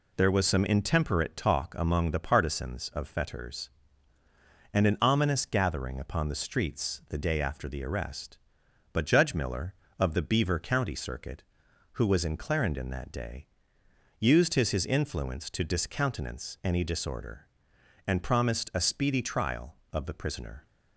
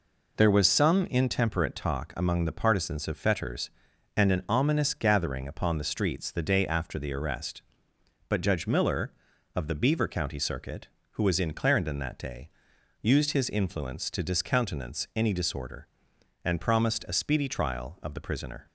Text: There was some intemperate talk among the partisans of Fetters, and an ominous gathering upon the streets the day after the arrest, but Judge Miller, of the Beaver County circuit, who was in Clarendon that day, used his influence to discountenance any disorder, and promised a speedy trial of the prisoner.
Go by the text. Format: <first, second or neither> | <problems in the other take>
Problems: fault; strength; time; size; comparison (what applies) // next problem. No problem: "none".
second | says "his" twice; at 14.6 s